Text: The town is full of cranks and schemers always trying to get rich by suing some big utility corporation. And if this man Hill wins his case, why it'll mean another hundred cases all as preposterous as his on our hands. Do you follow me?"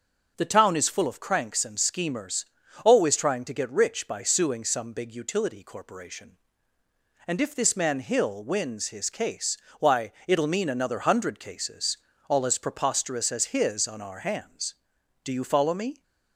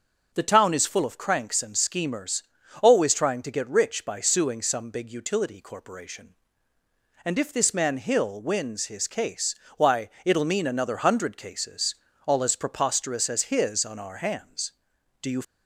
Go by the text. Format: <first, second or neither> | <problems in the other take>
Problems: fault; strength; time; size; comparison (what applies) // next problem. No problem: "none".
first | starts louder than the rest; noticeable; until 1.3 s; 6 dB; noticeable in the first // pauses between "schemers" and "always"; at 2.4 s; 0.42 s long; also in the first // pauses between "why" and "it'll"; slight; at 10.0 s; 0.16 s long; slight in the first // pauses between "cases" and "all"; slight; at 11.9 s; 0.30 s long; slight in the first // stops before "follow me"; at 15.4 s